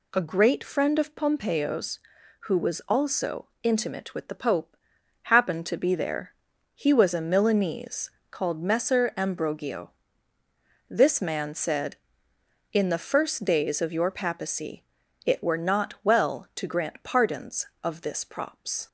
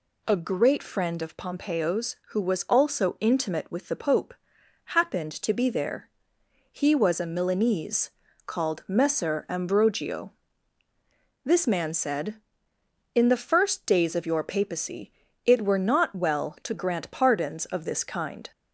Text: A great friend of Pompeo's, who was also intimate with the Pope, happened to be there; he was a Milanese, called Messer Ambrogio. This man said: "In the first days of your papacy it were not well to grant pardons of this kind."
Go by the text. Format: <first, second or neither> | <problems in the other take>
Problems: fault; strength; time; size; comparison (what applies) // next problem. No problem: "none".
second | pauses between "also" and "intimate"; slight; at 3.4 s; 0.16 s long // pauses between "papacy" and "it"; at 14.8 s; 0.44 s long; slight in the second // says "props" for "kind"; at 18.2 s